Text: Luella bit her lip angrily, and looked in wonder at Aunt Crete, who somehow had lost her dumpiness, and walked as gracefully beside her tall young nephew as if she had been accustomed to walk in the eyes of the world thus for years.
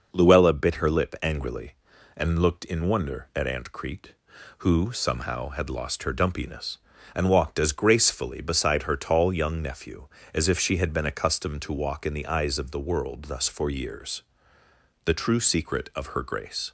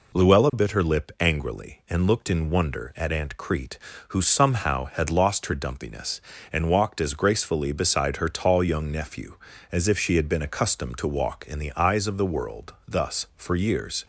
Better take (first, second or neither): second